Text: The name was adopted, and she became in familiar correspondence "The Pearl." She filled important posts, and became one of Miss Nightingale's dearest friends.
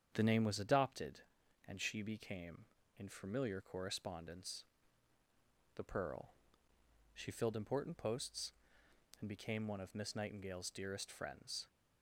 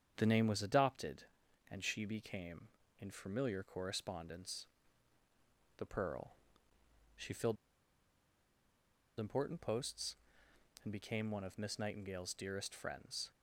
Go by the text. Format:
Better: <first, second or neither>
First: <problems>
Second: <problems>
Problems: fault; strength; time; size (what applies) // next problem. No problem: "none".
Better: first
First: starts louder than the rest; strong; until 1.1 s; 8 dB // pauses between "correspondence" and "The"; at 4.6 s; 1.1 s long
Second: starts louder than the rest; strong; until 1.1 s; 8 dB // pauses between "correspondence" and "The"; at 4.6 s; 1.1 s long // pauses between "filled" and "important"; strong; at 7.5 s; 1.6 s long